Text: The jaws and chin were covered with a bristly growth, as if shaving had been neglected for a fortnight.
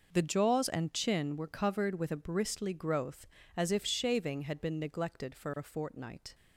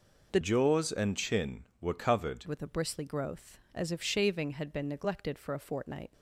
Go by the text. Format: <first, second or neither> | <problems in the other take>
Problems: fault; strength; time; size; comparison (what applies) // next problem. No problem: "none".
first | changes voice from "jaws" to "covered"; from 0.4 to 2.4 s; 2.0 s long